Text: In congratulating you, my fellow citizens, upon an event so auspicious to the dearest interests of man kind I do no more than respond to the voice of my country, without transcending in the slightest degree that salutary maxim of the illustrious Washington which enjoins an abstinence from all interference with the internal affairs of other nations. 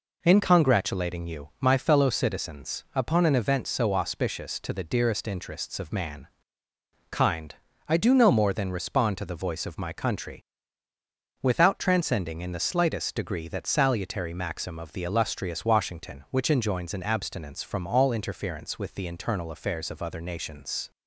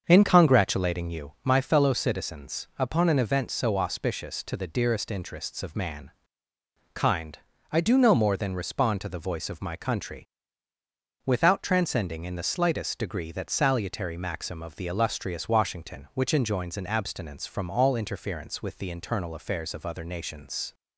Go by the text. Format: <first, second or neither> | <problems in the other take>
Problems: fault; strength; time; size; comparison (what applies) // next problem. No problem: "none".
first | starts louder than the rest; until 1.3 s; 6.5 dB // pauses between "man" and "kind"; noticeable; at 6.0 s; 0.82 s long; noticeable in the first // pauses between "kind" and "I"; slight; at 7.3 s; 0.34 s long; slight in the first